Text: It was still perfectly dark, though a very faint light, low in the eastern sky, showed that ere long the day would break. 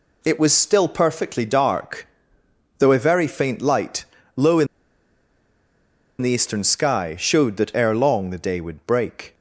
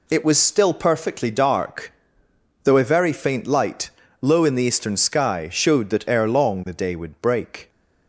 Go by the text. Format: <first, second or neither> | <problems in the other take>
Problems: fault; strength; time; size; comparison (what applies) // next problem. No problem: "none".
second | pauses between "in" and "the"; strong; at 4.6 s; 1.5 s long